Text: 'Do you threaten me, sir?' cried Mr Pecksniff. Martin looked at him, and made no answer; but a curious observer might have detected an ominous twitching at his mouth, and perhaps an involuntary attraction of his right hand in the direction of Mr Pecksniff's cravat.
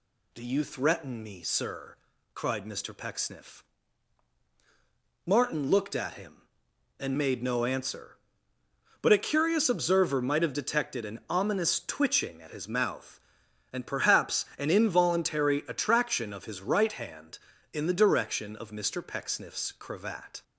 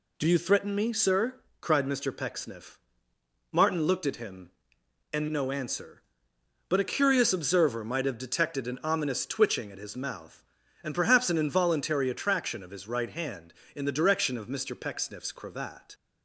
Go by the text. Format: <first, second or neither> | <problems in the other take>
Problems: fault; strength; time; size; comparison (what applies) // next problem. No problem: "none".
first | skips "made"; at 5.2 s